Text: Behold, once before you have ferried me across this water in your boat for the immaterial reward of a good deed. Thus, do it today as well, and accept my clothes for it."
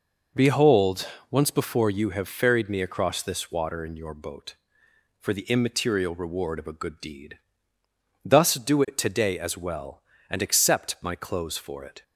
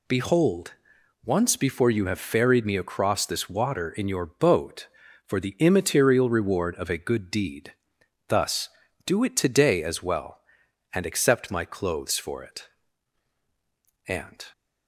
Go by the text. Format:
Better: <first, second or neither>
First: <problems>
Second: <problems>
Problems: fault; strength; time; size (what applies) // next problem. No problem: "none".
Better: first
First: none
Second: goes on to say "And"; slight; from 14.0 s on; 0.36 s long